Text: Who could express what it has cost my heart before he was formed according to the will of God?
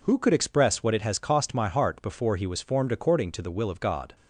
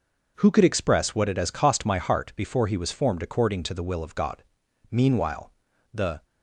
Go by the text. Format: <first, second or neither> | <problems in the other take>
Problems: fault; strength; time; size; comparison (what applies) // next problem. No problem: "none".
first | goes on to say "Meanwhile the"; from 4.9 s on; 1.3 s long